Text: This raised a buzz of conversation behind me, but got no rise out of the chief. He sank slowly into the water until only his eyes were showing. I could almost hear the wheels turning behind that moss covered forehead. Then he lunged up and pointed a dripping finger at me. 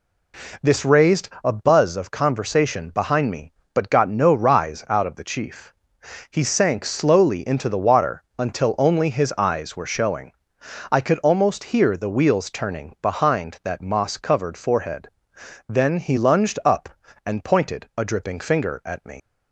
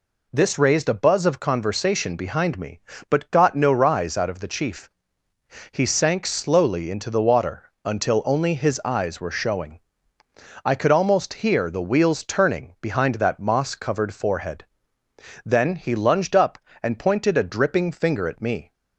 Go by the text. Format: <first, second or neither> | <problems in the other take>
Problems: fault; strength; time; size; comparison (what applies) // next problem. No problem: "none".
second | pauses between "raised" and "a"; slight; at 1.2 s; 0.16 s long // pauses between "water" and "until"; slight; at 8.2 s; 0.16 s long // leaves "me" unfinished; at 19.1 s; 75 ms